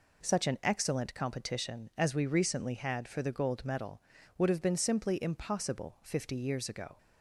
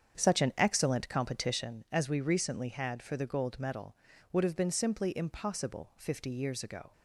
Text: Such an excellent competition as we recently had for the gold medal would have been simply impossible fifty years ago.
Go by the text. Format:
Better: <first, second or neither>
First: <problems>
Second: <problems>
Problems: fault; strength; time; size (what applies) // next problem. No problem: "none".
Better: first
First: none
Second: starts louder than the rest; strong; until 1.9 s; 8 dB